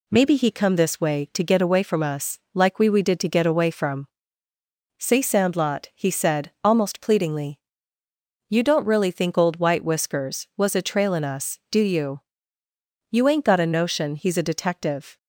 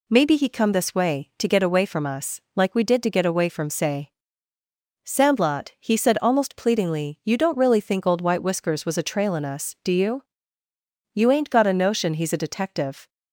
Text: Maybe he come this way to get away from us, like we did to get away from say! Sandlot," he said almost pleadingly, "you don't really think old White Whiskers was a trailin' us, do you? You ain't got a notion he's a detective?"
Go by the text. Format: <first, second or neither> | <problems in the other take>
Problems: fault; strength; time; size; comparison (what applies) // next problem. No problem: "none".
second | says "we" twice; at 2.8 s // pauses between "from" and "say"; noticeable; at 4.0 s; 0.90 s long